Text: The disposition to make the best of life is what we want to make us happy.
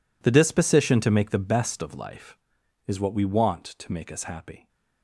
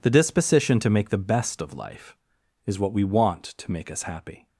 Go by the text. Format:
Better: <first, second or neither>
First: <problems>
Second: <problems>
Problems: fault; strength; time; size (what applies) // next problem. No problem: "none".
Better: second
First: gets quieter; strong; throughout; 17 dB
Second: none